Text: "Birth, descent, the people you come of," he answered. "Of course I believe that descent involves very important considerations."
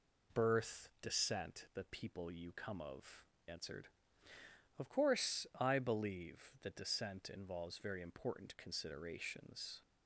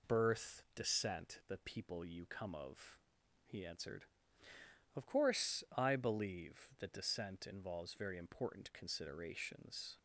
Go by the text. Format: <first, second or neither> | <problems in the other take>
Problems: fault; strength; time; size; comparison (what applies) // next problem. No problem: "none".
second | skips "he"; at 3.3 s